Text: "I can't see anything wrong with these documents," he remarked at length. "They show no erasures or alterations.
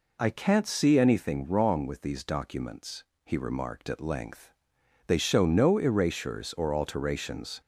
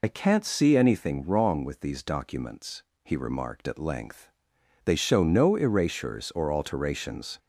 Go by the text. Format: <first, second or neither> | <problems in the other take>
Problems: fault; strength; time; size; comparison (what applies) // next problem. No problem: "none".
first | loses the start of "I"; at 0.0 s; 60 ms